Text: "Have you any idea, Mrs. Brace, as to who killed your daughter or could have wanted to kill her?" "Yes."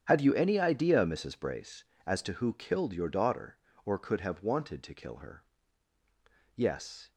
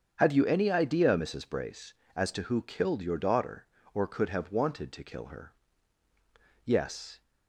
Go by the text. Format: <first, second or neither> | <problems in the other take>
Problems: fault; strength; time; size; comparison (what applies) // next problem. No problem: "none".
second | gets quieter; strong; throughout; 15 dB // starts louder than the rest; strong; until 1.0 s; 9 dB; strong in the second